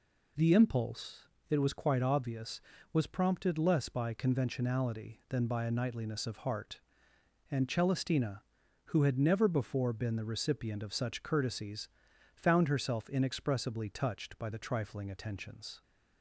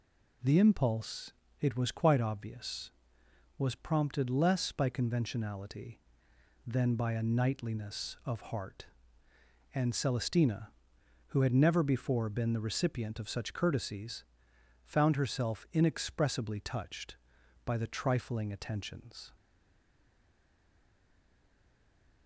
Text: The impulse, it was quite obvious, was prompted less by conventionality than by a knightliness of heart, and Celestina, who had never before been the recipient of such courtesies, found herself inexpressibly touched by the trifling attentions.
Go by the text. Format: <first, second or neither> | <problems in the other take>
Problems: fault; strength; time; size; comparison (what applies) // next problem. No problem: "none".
first | stays silent after the last word; strong; from 19.3 s on; 2.9 s long